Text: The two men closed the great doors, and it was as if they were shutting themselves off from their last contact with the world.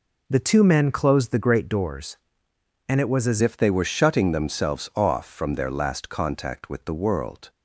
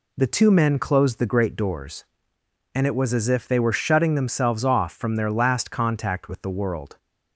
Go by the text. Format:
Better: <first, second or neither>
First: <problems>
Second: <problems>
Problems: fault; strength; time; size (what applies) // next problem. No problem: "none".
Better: second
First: changes voice at "if"; from 3.4 s on; 4.0 s long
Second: none